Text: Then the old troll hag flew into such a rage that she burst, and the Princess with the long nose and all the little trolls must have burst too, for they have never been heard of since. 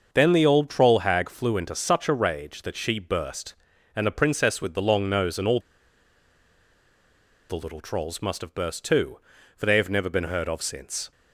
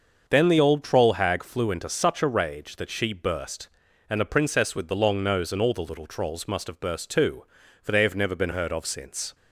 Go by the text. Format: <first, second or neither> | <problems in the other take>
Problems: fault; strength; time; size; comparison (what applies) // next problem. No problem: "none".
second | starts louder than the rest; until 1.1 s; 6.5 dB; also in the second // pauses between "all" and "the"; strong; at 5.6 s; 1.8 s long